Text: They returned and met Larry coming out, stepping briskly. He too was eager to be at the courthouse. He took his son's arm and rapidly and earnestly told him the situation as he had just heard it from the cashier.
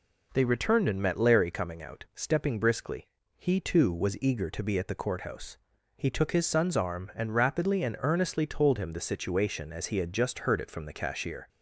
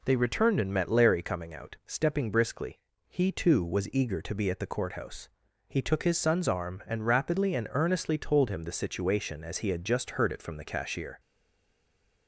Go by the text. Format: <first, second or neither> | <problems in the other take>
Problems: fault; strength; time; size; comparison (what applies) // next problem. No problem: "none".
first | stays silent after the last word; from 11.1 s on; 1.1 s long